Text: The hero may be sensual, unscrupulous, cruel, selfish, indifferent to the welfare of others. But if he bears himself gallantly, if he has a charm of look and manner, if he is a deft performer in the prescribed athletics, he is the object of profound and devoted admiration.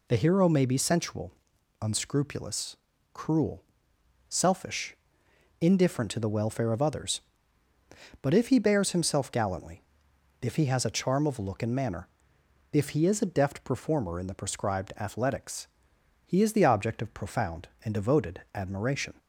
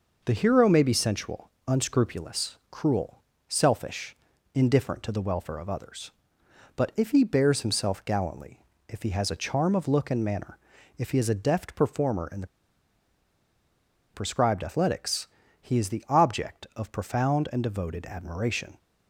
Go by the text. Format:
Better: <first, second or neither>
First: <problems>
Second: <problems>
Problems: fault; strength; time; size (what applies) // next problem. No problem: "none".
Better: first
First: none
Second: pauses between "the" and "prescribed"; strong; at 12.4 s; 1.6 s long